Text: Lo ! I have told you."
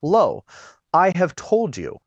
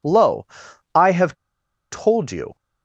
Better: first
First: none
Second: pauses between "have" and "told"; noticeable; at 1.3 s; 0.55 s long

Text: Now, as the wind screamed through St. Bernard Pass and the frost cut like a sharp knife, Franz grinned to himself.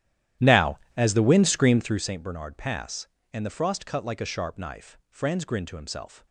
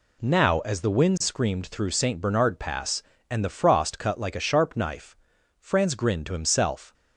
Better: second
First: starts louder than the rest; strong; until 2.1 s; 12 dB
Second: none

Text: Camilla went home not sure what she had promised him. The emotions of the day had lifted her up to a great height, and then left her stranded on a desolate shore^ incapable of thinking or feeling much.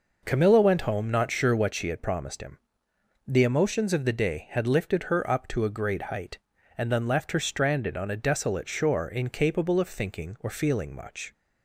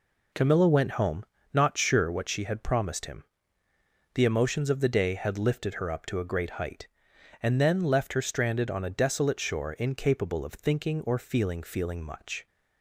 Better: first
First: none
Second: pauses between "home" and "not"; slight; at 1.2 s; 0.26 s long // says "feeling" twice; at 11.6 s

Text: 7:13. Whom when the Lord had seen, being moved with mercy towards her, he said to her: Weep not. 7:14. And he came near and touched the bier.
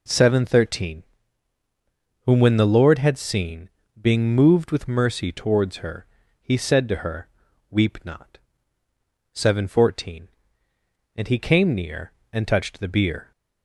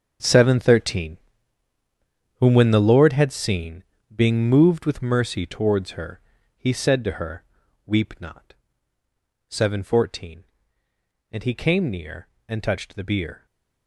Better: first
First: none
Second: gets quieter; strong; throughout; 13 dB

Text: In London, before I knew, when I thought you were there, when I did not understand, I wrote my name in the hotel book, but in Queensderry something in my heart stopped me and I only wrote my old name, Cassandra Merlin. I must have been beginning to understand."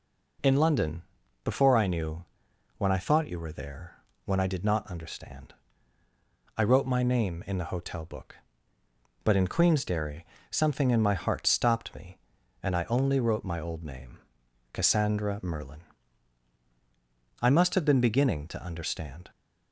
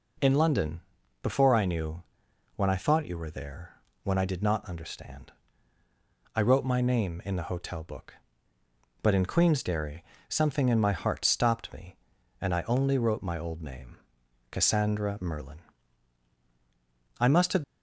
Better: first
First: pauses between "Queensderry" and "something"; slight; at 10.2 s; 0.26 s long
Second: pauses between "Queensderry" and "something"; slight; at 10.0 s; 0.26 s long // stops before "been beginning to understand"; at 17.6 s

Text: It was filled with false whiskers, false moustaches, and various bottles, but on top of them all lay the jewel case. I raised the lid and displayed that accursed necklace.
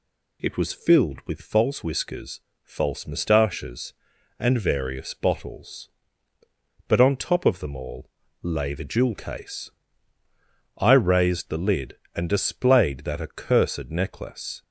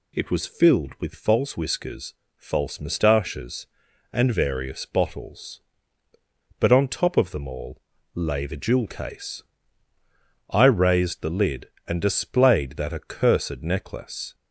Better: neither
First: pauses between "all" and "lay"; slight; at 8.0 s; 0.35 s long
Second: pauses between "all" and "lay"; slight; at 7.7 s; 0.36 s long

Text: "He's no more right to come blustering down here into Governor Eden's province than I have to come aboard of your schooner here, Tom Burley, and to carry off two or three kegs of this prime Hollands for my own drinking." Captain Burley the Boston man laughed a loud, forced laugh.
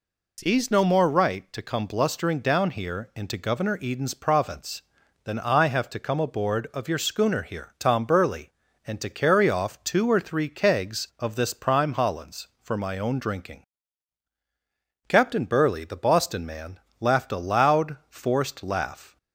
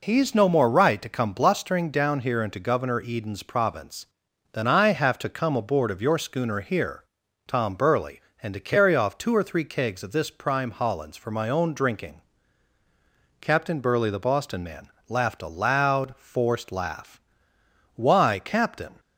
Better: first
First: pauses between "man" and "laughed"; slight; at 16.7 s; 0.22 s long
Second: pauses between "man" and "laughed"; slight; at 14.8 s; 0.18 s long // goes on to say "Why Captain"; noticeable; from 17.9 s on; 1.0 s long

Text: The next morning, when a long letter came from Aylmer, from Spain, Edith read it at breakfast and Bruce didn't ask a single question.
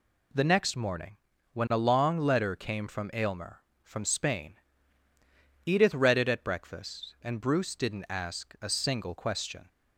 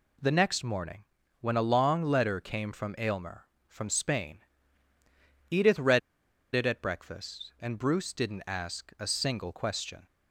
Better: first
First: none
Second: pauses between "read" and "it"; noticeable; at 5.9 s; 0.55 s long

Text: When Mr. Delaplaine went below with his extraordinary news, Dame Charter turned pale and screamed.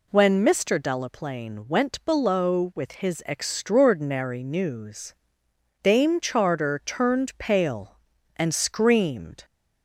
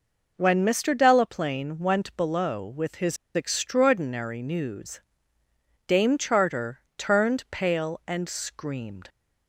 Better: first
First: none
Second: pauses between "his" and "extraordinary"; slight; at 3.1 s; 0.18 s long // pauses between "Charter" and "turned"; slight; at 6.8 s; 0.16 s long

